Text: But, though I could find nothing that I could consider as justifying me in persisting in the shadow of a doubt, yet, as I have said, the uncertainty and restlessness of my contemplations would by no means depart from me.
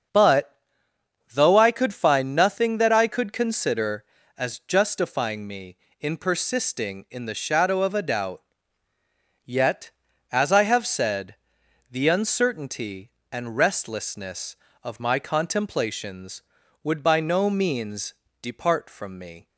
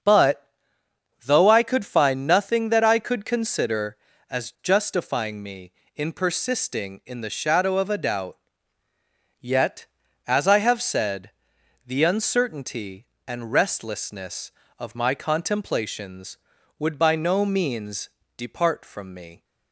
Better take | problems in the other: neither | starts louder than the rest; the same in both // pauses between "means" and "depart"; slight; the same in both

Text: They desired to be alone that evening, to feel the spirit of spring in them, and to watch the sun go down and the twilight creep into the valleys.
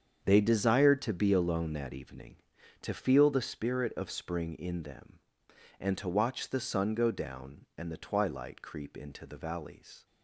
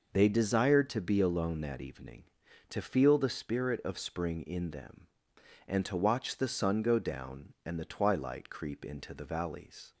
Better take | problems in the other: second | gets quieter; strong; throughout; 12 dB

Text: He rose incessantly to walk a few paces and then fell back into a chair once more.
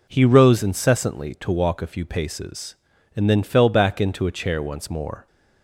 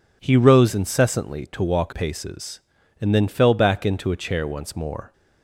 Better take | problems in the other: first | skips "a few"; at 1.9 s

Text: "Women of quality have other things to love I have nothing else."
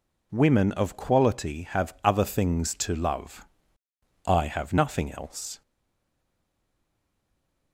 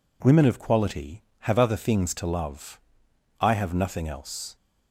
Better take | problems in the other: second | pauses between "love" and "I"; noticeable; at 3.4 s; 0.80 s long; noticeable in the second // stays silent after the last word; from 5.6 s on; 2.1 s long

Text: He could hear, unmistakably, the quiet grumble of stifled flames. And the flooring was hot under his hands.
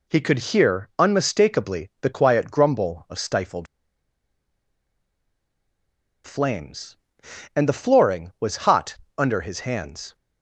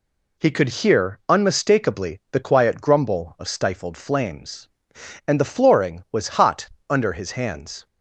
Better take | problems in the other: second | pauses between "stifled" and "flames"; strong; at 3.6 s; 2.5 s long // pauses between "hot" and "under"; slight; at 8.9 s; 0.22 s long; slight in the second

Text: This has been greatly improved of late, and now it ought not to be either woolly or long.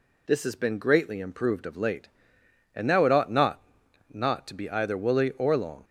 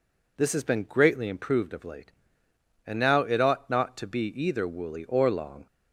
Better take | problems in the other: second | says "not" twice; at 4.1 s

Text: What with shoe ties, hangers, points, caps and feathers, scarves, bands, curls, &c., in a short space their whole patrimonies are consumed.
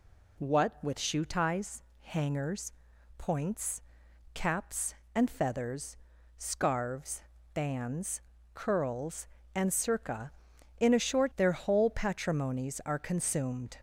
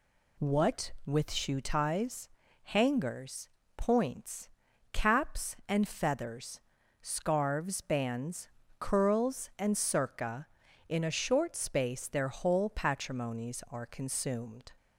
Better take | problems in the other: second | skips "space"; at 11.3 s

